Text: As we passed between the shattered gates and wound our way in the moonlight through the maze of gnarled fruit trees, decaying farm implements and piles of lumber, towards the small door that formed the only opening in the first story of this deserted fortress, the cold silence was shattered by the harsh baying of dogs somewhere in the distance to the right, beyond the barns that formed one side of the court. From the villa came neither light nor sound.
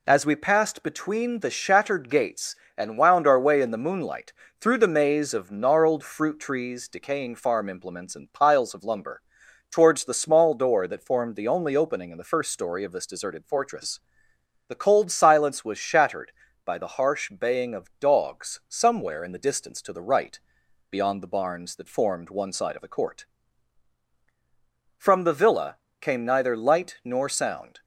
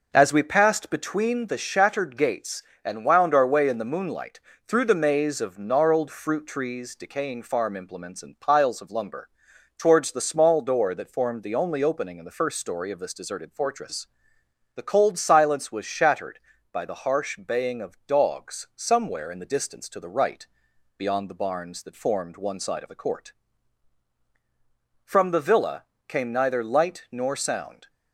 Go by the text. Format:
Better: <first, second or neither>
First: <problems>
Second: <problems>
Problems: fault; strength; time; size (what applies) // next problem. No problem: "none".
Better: first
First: pauses between "moonlight" and "through"; slight; at 4.3 s; 0.26 s long // pauses between "villa" and "came"; slight; at 25.7 s; 0.24 s long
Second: starts louder than the rest; noticeable; until 1.4 s; 5.5 dB // pauses between "moonlight" and "through"; slight; at 4.3 s; 0.26 s long // pauses between "villa" and "came"; slight; at 25.8 s; 0.24 s long